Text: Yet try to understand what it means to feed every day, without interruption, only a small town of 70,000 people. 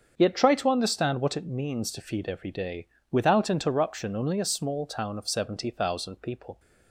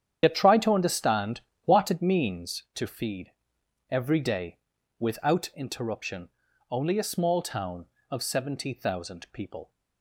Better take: first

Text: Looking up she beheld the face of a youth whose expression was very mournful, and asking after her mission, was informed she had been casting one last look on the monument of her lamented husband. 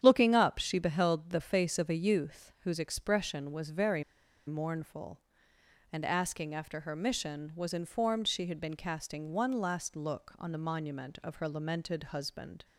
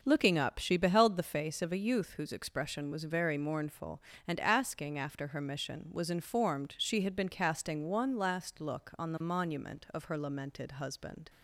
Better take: second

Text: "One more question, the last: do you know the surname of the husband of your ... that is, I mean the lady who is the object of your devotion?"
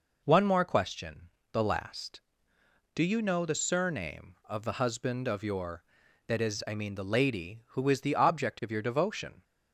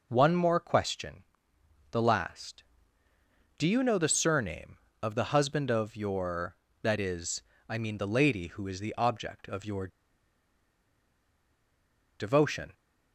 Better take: first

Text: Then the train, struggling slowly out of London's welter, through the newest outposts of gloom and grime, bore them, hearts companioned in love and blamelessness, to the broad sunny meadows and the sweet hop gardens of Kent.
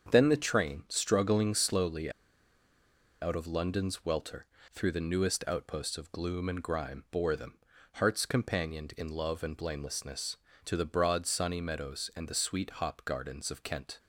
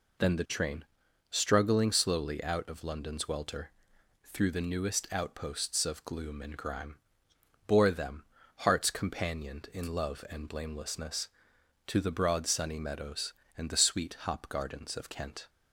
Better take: second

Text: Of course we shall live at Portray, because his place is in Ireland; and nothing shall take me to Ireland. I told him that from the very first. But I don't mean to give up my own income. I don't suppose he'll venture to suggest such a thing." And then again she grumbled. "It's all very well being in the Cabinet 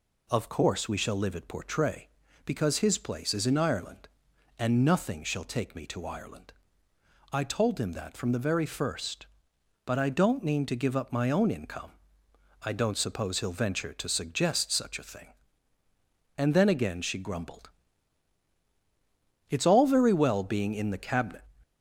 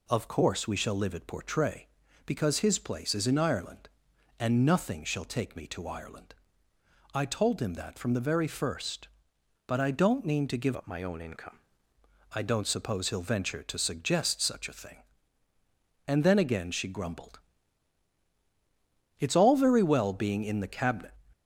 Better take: first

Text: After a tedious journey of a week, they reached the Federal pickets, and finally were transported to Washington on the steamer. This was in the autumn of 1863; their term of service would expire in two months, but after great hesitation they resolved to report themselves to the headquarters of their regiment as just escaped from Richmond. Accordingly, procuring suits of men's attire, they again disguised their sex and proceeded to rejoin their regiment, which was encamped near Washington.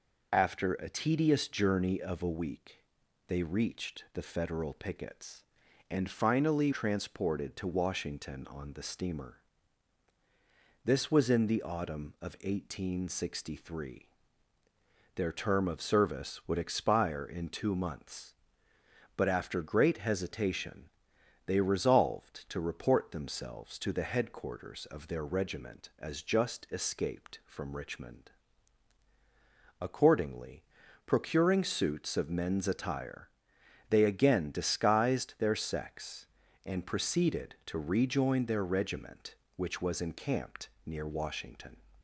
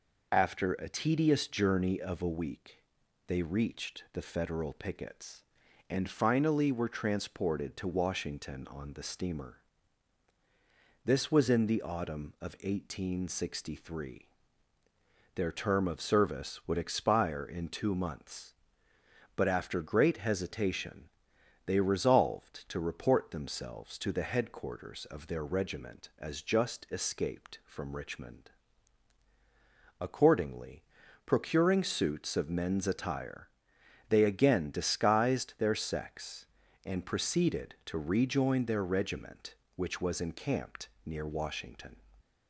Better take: second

